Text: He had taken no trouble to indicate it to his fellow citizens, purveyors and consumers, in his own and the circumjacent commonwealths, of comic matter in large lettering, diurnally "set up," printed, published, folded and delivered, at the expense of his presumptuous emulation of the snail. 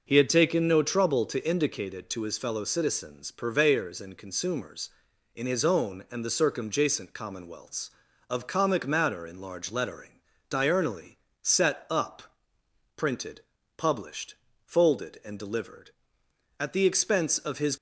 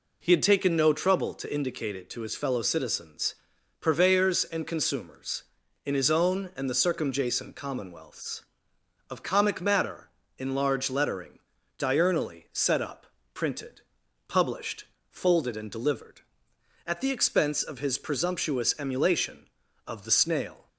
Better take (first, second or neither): second